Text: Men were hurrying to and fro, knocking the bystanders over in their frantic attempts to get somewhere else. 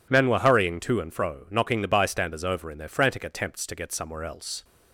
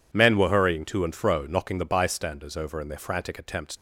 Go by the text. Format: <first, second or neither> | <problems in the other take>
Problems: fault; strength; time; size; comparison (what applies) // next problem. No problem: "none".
first | stops before "to get somewhere else"; at 3.7 s